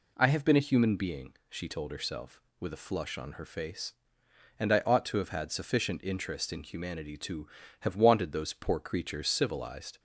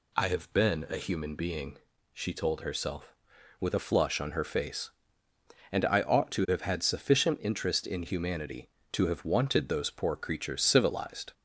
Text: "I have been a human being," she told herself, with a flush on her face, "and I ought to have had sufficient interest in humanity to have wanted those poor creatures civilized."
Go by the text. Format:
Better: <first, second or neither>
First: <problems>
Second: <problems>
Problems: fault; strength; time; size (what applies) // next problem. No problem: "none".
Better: neither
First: none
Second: none